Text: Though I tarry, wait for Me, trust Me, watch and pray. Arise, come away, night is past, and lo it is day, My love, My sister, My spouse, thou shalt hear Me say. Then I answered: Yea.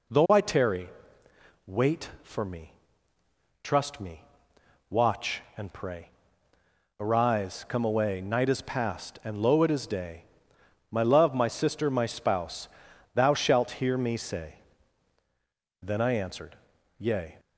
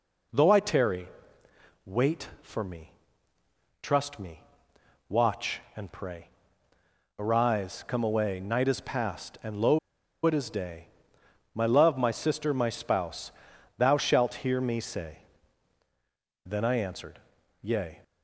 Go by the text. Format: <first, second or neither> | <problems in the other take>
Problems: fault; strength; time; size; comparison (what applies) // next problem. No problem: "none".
first | pauses between "lo" and "it"; noticeable; at 9.7 s; 0.46 s long